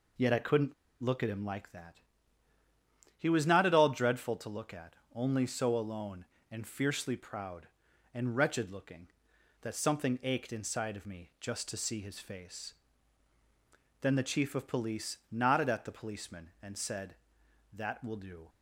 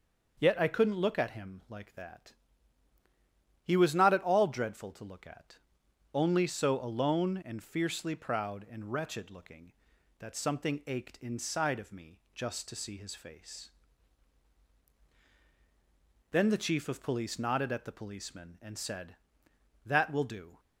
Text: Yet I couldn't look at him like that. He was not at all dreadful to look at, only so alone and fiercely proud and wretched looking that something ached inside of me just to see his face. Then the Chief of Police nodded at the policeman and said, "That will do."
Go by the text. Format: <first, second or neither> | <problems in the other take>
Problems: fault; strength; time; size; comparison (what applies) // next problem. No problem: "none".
second | pauses between "couldn't" and "look"; slight; at 0.7 s; 0.29 s long